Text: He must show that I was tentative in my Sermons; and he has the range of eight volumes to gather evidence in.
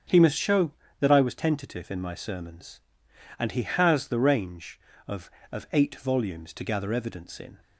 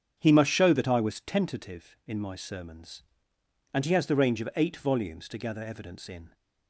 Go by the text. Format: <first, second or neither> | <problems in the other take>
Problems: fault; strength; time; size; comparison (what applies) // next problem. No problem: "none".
second | starts louder than the rest; strong; until 1.3 s; 8 dB; strong in the second // says "of" twice; at 5.5 s